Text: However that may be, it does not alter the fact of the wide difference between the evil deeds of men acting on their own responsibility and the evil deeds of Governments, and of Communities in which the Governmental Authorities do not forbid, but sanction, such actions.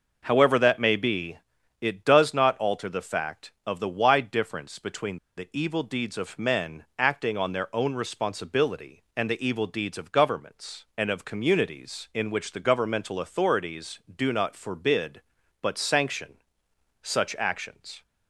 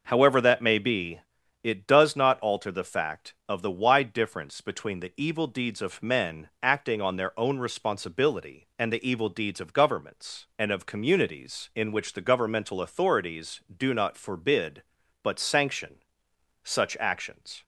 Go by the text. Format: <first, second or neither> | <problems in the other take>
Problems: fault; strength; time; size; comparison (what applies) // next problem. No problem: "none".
second | pauses between "between" and "the"; slight; at 5.1 s; 0.19 s long